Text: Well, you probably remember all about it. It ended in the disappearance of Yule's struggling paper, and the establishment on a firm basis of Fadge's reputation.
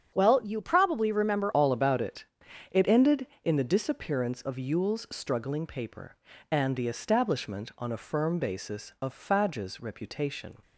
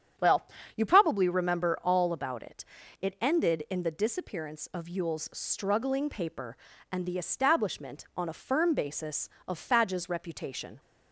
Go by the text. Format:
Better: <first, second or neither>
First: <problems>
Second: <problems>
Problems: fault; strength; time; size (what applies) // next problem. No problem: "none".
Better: second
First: starts louder than the rest; strong; until 1.1 s; 8 dB // changes voice at "all"; from 1.5 s on; 9.0 s long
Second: starts louder than the rest; strong; until 1.4 s; 8 dB